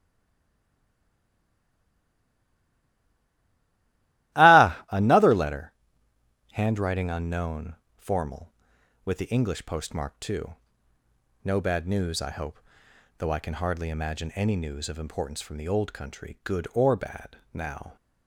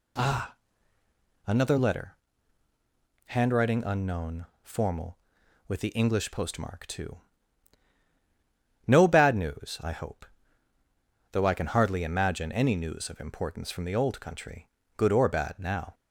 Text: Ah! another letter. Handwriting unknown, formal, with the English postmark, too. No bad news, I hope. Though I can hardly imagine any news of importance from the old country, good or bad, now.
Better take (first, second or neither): second